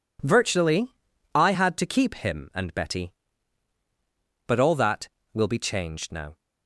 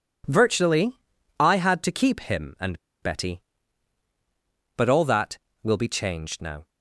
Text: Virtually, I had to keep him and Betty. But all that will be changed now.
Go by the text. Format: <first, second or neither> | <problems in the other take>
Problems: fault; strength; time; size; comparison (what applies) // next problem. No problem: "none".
first | pauses between "and" and "Betty"; slight; at 2.7 s; 0.23 s long